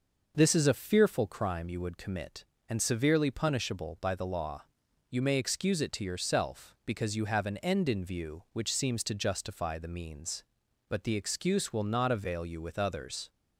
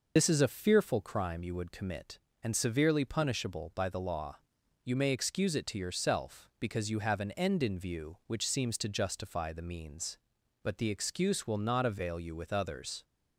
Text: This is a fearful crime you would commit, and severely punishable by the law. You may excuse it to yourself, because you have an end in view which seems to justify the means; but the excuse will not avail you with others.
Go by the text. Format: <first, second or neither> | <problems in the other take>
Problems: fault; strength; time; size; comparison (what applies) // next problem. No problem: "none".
first | loses the start of "This"; at 0.1 s; 70 ms